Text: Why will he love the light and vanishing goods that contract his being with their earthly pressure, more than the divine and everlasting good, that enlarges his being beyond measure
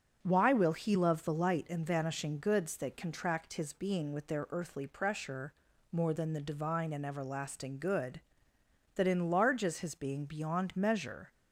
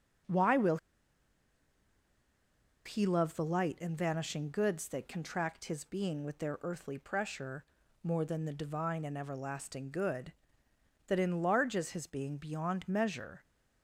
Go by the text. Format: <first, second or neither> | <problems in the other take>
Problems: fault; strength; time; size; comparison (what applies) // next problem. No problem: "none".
first | starts louder than the rest; until 3.3 s; 6 dB // pauses between "will" and "he"; strong; at 0.7 s; 2.0 s long